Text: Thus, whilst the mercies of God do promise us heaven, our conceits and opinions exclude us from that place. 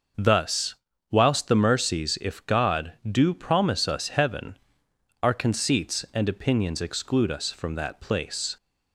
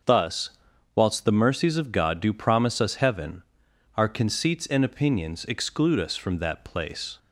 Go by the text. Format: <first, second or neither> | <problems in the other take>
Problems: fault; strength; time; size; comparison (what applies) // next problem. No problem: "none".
second | starts louder than the rest; noticeable; until 1.5 s; 6 dB; also in the second // says "if" for "of"; at 2.2 s